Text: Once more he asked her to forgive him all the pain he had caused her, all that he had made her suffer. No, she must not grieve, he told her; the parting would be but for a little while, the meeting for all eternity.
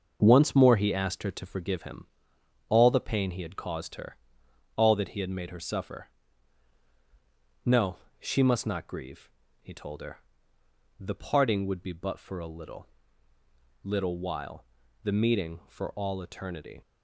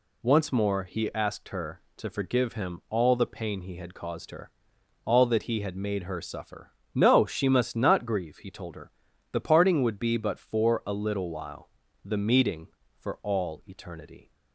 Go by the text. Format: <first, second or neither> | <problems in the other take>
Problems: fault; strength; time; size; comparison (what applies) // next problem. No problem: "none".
second | starts louder than the rest; until 1.2 s; 6.5 dB // pauses between "him" and "all"; noticeable; at 2.0 s; 0.64 s long // says "little" twice; at 13.8 s